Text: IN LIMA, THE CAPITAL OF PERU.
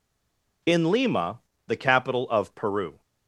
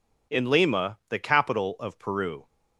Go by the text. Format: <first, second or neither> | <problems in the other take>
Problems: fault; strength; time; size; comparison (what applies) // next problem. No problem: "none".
second | stays silent before the first word; slight; until 0.6 s; 0.6 s long